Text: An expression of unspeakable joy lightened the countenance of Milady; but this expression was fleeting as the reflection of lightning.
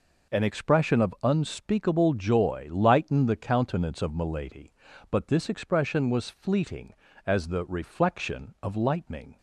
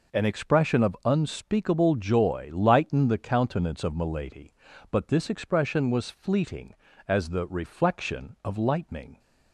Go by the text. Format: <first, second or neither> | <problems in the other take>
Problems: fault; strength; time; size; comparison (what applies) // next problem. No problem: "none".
neither | none